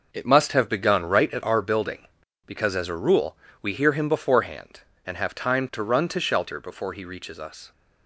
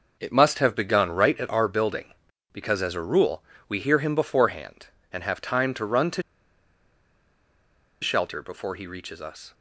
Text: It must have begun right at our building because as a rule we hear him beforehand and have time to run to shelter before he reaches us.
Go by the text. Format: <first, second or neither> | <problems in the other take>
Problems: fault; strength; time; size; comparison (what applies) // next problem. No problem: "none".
first | pauses between "rule" and "we"; slight; at 3.4 s; 0.26 s long; slight in the first // pauses between "to" and "shelter"; strong; at 6.2 s; 1.7 s long